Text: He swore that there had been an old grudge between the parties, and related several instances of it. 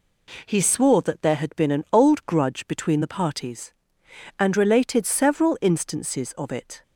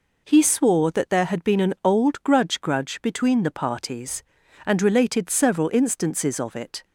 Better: first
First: none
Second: says "grudge" twice; at 2.6 s

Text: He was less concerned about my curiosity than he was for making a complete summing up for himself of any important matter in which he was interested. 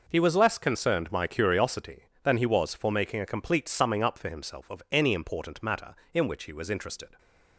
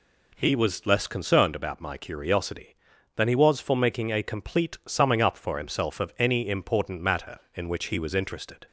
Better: second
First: skips "about"; at 1.1 s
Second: none

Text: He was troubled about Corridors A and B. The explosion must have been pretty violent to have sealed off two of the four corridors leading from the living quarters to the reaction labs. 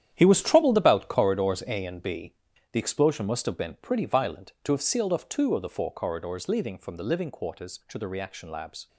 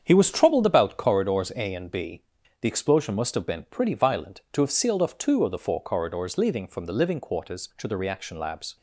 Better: second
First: gets quieter; strong; throughout; 11 dB // starts louder than the rest; strong; until 1.1 s; 10 dB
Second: starts louder than the rest; strong; until 1.0 s; 7.5 dB

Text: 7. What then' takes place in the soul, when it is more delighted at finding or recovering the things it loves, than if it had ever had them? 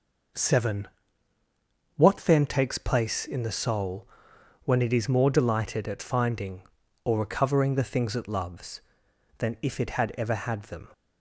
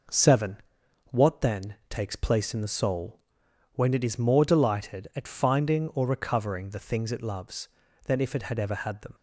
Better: neither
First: none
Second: none

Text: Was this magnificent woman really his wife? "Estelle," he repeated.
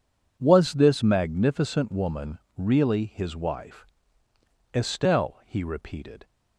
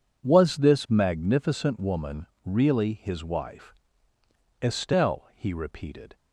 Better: neither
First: pauses between "woman" and "really"; slight; at 2.3 s; 0.18 s long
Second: pauses between "woman" and "really"; slight; at 2.2 s; 0.18 s long

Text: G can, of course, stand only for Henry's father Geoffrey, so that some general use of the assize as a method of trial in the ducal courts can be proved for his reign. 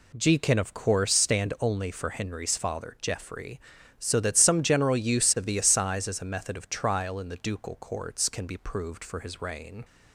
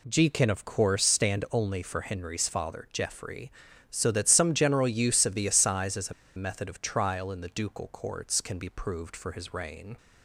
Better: first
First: none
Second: pauses between "a" and "method"; slight; at 6.1 s; 0.24 s long

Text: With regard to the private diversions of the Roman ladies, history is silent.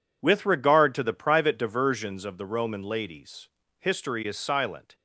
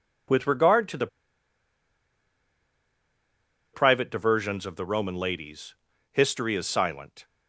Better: first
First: none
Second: pauses between "the" and "private"; strong; at 1.0 s; 2.6 s long

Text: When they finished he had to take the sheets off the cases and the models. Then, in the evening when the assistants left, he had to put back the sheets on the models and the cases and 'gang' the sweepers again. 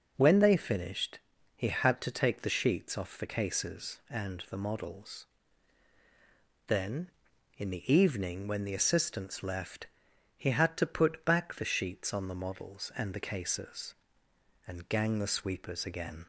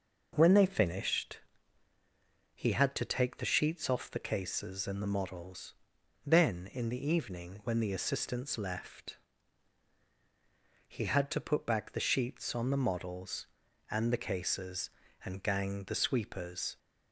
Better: first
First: pauses between "finished" and "he"; at 1.2 s; 0.38 s long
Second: pauses between "finished" and "he"; at 1.3 s; 1.1 s long // stops before "again"; at 16.7 s

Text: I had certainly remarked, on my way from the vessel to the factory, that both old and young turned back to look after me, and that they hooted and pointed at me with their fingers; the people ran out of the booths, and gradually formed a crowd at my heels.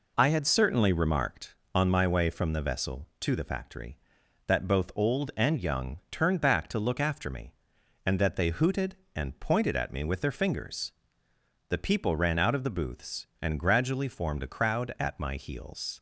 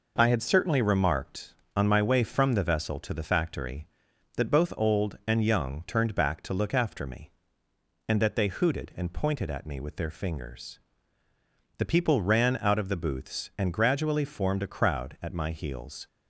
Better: neither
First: none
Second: none

